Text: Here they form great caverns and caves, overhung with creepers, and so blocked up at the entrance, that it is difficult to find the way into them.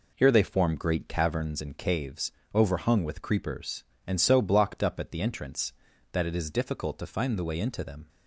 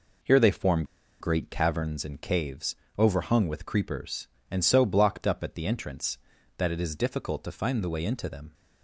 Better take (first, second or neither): first